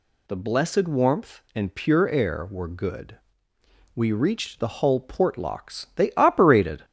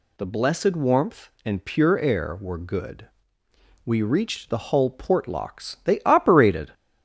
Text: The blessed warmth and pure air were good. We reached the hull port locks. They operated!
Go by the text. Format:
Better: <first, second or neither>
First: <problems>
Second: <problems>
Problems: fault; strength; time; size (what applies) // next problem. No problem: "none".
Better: neither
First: none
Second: none